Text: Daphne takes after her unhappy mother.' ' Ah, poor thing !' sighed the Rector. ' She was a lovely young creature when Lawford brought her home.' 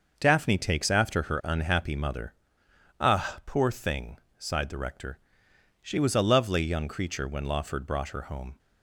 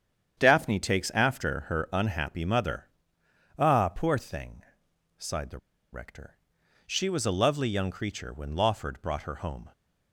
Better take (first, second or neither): first